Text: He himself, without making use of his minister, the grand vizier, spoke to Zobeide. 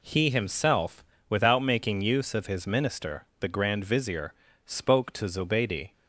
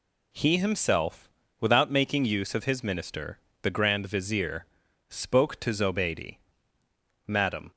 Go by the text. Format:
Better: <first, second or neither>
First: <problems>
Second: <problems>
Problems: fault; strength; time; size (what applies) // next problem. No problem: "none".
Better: first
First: none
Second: goes on to say "Madam"; slight; from 7.2 s on; 0.44 s long